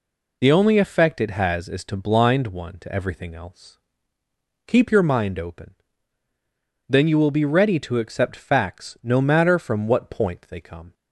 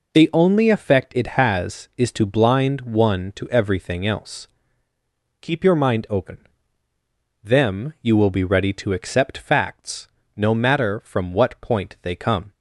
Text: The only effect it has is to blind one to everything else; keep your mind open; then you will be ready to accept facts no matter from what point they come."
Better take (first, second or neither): first